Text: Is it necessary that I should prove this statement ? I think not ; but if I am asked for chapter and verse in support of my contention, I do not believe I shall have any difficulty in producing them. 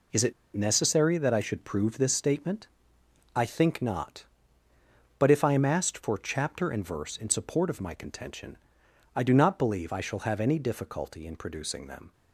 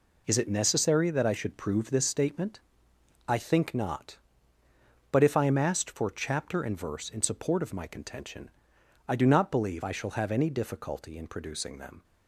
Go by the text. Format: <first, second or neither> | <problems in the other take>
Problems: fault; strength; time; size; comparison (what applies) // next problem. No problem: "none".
second | pauses between "it" and "necessary"; slight; at 0.3 s; 0.21 s long